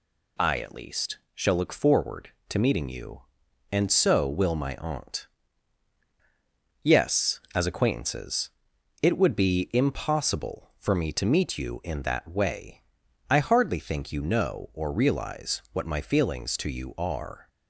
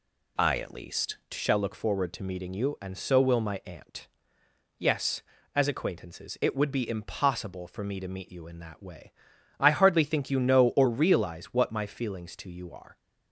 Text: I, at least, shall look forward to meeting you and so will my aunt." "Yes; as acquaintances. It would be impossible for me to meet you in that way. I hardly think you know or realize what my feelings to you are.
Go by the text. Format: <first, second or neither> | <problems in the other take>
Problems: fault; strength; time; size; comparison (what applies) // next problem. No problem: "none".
first | changes voice at "shall"; from 1.3 s on; 11.6 s long